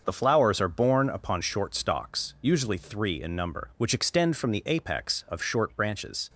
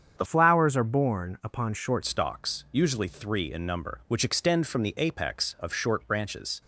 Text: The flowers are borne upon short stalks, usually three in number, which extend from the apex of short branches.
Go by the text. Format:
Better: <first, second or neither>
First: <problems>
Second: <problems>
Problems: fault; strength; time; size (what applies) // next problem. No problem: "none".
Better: first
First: starts louder than the rest; until 1.0 s; 6.5 dB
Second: starts louder than the rest; strong; until 1.1 s; 7.5 dB // changes voice from "flowers" to "short"; from 0.2 to 2.0 s; 1.8 s long